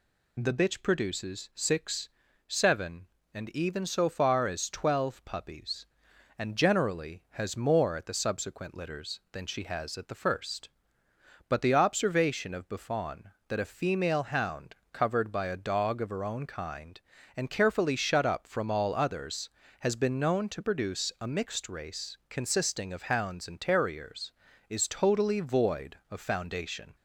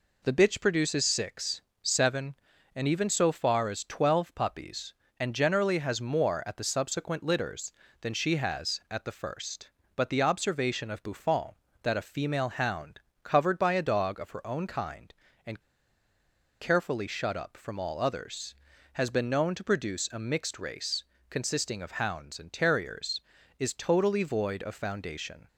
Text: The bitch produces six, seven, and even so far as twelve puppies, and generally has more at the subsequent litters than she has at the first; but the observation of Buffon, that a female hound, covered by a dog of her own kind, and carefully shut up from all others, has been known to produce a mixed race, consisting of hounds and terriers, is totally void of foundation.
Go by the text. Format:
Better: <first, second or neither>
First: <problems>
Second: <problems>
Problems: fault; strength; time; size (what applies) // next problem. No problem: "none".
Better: first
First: none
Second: pauses between "and" and "carefully"; at 15.6 s; 1.0 s long